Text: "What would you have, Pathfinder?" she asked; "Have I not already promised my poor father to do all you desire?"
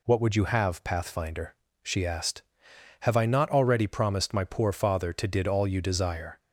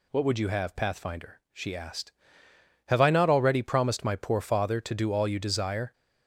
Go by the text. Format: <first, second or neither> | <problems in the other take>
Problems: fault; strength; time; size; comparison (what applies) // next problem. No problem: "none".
second | says "did" for "do"; at 5.2 s